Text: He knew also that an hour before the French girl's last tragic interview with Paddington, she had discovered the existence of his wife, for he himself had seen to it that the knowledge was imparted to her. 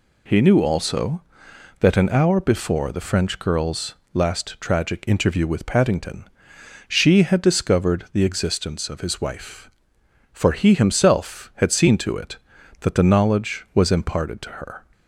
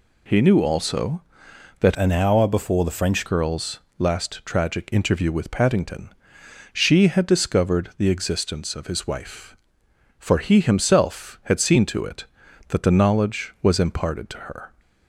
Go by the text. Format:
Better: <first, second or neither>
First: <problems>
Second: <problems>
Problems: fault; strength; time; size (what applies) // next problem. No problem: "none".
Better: first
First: pauses between "girl's" and "last"; slight; at 3.9 s; 0.18 s long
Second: changes voice from "an" to "French"; from 1.9 to 3.2 s; 1.3 s long // pauses between "girl's" and "last"; slight; at 3.7 s; 0.18 s long